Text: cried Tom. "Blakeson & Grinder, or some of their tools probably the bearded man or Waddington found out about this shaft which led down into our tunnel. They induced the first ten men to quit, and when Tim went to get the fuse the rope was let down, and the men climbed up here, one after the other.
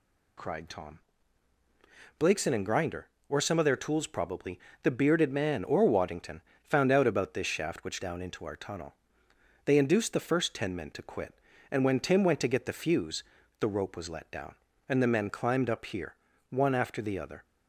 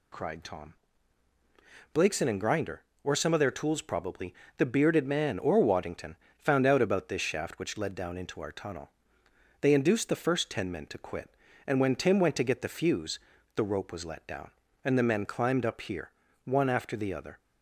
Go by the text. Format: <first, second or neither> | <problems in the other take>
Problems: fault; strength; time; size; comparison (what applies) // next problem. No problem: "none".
second | pauses between "probably" and "the"; slight; at 4.5 s; 0.26 s long; slight in the second // pauses between "Waddington" and "found"; slight; at 6.4 s; 0.20 s long; slight in the second // skips "led"; at 8.0 s // pauses between "fuse" and "the"; at 13.2 s; 0.38 s long; also in the second